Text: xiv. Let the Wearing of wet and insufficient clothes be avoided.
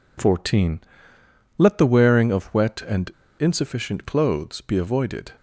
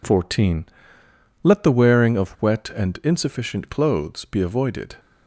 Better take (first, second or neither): second